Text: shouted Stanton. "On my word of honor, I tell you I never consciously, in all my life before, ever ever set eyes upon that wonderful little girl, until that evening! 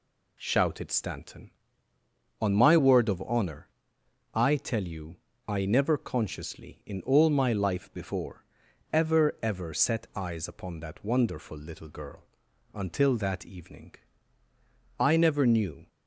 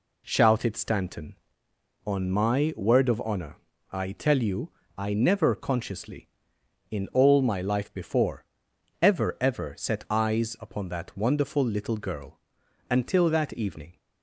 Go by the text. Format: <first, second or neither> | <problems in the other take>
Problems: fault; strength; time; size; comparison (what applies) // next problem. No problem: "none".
second | pauses between "you" and "I"; slight; at 5.1 s; 0.32 s long; slight in the second // goes on to say "I never knew"; noticeable; from 14.9 s on; 0.88 s long